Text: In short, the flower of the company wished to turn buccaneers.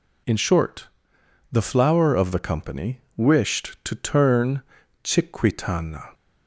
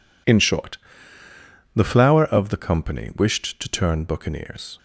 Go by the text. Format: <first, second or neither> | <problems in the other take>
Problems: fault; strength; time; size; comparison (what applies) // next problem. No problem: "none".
second | pauses between "company" and "wished"; slight; at 2.9 s; 0.16 s long // says "chiquitana" for "buccaneers"; at 5.0 s